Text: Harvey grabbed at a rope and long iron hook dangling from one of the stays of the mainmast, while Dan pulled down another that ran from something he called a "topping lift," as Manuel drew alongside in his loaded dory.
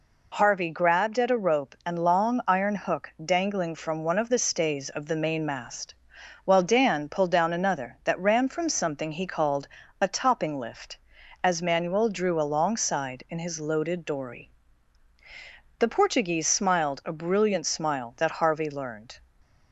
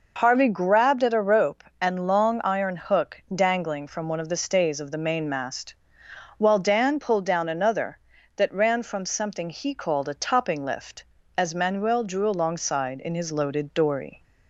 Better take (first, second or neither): second